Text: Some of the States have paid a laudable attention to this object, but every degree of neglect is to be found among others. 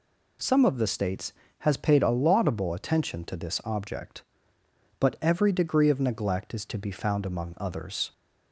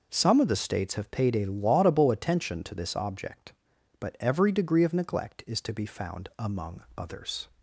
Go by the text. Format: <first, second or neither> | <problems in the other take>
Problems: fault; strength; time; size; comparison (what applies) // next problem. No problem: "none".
second | says "has" for "have"; at 1.5 s